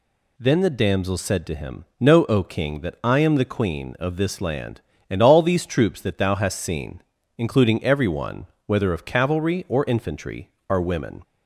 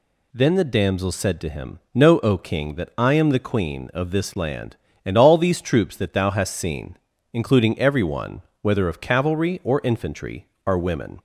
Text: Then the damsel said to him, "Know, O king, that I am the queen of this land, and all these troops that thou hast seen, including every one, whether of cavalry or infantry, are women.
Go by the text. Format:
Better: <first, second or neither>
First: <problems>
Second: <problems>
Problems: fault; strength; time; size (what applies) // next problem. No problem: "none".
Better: neither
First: none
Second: none